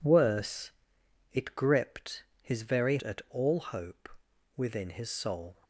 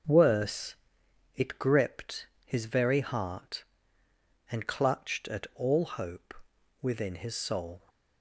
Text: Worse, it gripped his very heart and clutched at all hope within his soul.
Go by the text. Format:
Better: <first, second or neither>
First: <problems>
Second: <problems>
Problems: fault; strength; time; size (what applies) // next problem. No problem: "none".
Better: second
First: pauses between "gripped" and "his"; slight; at 2.2 s; 0.18 s long // skips "heart and clutched"; at 3.0 s // pauses between "hope" and "within"; noticeable; at 4.0 s; 0.48 s long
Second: pauses between "gripped" and "his"; slight; at 2.2 s; 0.18 s long // pauses between "hope" and "within"; noticeable; at 6.3 s; 0.48 s long